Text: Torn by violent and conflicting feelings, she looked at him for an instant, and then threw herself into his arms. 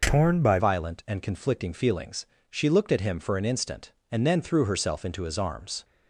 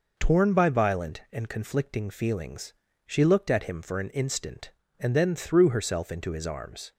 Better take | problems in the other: second | changes voice at "violent"; from 0.5 s on; 5.3 s long

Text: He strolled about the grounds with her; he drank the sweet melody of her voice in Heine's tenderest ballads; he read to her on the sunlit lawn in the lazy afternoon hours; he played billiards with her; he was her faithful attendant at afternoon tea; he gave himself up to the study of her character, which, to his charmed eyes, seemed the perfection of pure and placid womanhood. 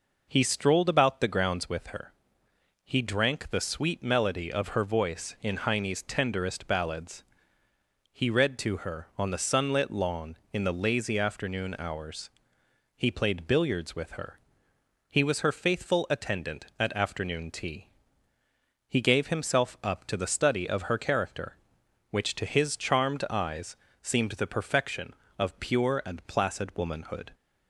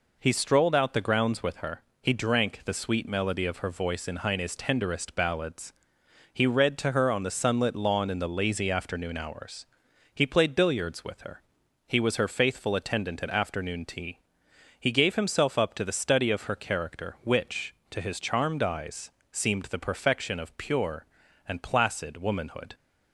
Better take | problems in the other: first | says "out" for "about"; at 0.7 s

